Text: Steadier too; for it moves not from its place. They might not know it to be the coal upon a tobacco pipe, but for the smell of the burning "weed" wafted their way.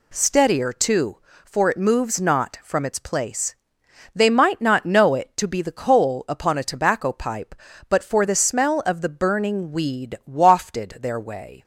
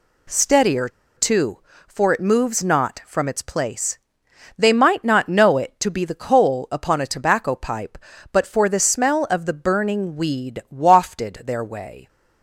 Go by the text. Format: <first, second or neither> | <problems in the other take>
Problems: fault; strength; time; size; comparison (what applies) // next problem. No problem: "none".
first | pauses between "Steadier" and "too"; slight; at 0.9 s; 0.26 s long